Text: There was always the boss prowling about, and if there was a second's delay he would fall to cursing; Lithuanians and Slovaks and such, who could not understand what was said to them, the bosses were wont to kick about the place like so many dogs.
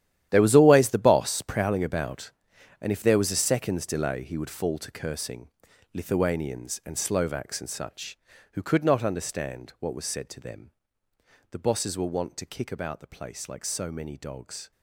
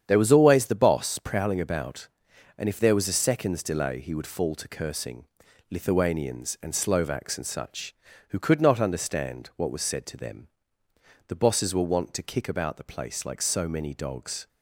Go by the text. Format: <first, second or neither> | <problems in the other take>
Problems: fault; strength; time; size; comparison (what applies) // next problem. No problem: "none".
second | gets quieter; strong; throughout; 14.5 dB // starts louder than the rest; strong; until 1.3 s; 11.5 dB; strong in the second